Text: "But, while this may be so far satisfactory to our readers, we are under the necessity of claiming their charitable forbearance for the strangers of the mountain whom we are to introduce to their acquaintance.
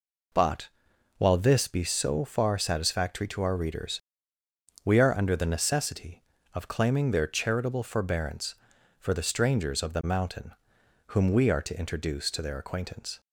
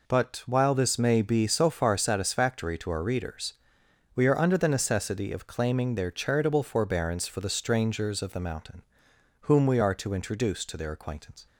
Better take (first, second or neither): second